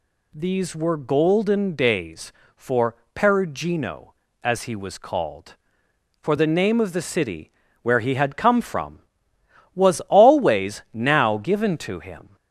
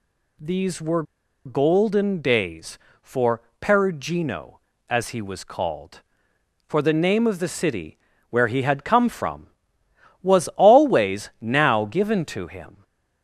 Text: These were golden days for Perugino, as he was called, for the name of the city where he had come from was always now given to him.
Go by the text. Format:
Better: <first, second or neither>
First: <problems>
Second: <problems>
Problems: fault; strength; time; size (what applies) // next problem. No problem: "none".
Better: first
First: pauses between "for" and "Perugino"; slight; at 2.9 s; 0.18 s long // pauses between "city" and "where"; slight; at 7.5 s; 0.30 s long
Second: pauses between "were" and "golden"; at 1.0 s; 0.42 s long // pauses between "for" and "Perugino"; slight; at 3.4 s; 0.18 s long // pauses between "city" and "where"; slight; at 7.9 s; 0.32 s long